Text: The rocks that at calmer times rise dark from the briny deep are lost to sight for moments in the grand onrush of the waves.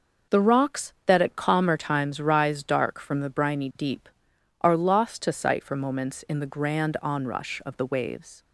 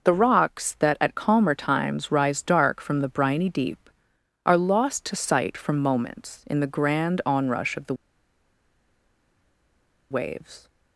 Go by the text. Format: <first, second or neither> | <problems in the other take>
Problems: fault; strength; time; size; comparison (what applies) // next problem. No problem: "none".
first | pauses between "the" and "waves"; strong; at 7.9 s; 2.1 s long